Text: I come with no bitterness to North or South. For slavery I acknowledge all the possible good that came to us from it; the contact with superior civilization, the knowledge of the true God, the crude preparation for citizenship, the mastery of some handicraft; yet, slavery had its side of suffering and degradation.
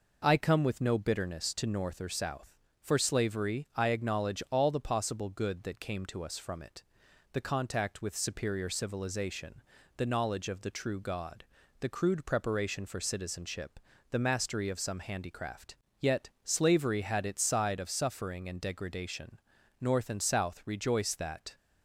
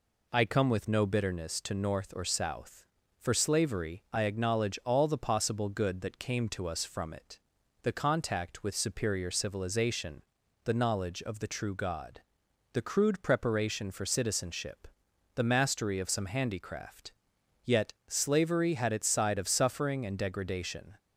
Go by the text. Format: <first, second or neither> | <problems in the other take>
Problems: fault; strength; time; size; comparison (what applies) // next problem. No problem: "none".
second | goes on to say "North and South rejoice that"; strong; from 19.8 s on; 1.7 s long